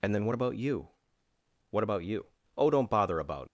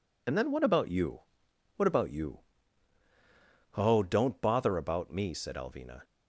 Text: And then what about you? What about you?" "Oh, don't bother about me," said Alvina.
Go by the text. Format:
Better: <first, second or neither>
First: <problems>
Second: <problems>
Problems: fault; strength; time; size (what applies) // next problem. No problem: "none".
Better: second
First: stops before "me said Alvina"; at 3.4 s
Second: none